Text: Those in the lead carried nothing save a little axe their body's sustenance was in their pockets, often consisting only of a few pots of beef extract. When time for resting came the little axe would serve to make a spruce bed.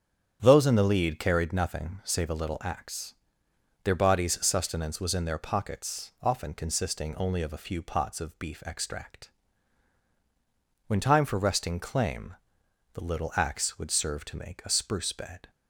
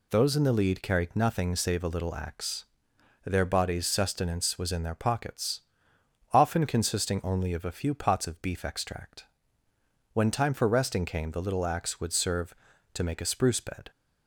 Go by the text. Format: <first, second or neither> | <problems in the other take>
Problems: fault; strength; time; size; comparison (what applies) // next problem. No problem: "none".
second | starts louder than the rest; strong; until 1.4 s; 9 dB // pauses between "axe" and "their"; noticeable; at 3.1 s; 0.70 s long; noticeable in the second // says "claim" for "came"; at 11.7 s